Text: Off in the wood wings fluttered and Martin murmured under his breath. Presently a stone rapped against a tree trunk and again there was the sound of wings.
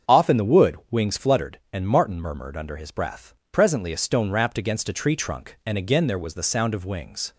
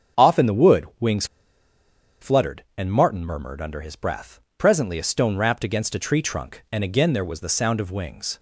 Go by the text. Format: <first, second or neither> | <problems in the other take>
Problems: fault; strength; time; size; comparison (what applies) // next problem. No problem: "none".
first | starts louder than the rest; strong; until 2.2 s; 7 dB; strong in the first // pauses between "wings" and "fluttered"; noticeable; at 1.2 s; 0.96 s long